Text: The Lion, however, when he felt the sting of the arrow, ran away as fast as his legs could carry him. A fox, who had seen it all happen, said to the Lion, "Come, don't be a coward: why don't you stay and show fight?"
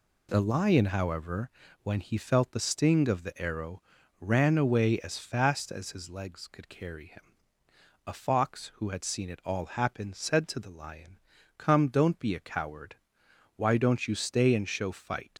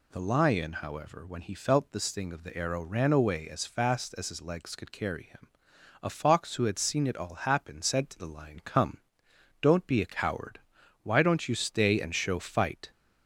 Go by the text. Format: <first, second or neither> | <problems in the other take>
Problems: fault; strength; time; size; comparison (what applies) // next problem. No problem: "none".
second | leaves "fight" unfinished; at 15.3 s; 105 ms